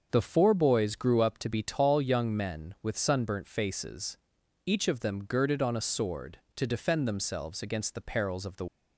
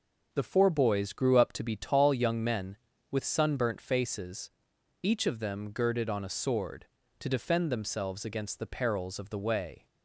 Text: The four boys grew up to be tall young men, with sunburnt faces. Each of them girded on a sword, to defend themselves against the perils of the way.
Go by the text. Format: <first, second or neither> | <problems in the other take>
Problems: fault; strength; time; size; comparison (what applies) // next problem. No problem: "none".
second | starts louder than the rest; until 1.1 s; 6.5 dB // stops before "way"; at 8.6 s